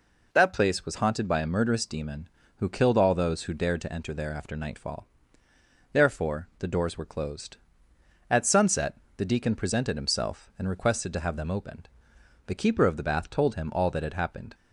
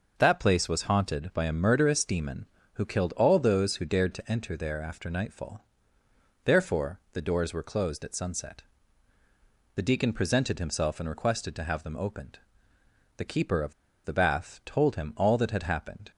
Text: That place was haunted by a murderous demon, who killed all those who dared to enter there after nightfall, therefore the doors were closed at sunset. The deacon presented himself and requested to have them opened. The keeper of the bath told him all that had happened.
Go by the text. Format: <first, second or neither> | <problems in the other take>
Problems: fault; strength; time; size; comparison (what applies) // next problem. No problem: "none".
first | pauses between "of" and "the"; slight; at 13.7 s; 0.30 s long